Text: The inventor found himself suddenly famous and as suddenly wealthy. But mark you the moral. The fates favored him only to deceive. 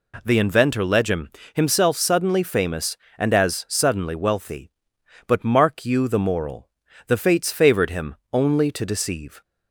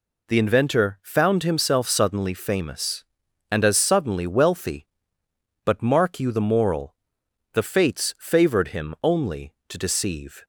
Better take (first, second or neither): second